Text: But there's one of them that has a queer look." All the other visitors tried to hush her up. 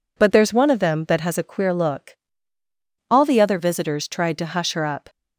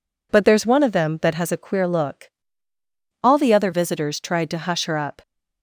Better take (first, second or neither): neither